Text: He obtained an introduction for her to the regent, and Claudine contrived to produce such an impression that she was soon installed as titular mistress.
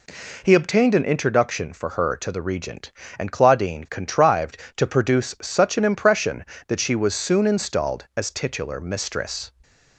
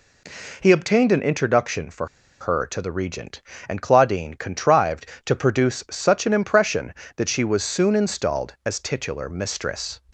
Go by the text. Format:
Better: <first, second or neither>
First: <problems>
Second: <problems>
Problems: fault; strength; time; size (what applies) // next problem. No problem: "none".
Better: first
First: none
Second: pauses between "for" and "her"; slight; at 2.0 s; 0.33 s long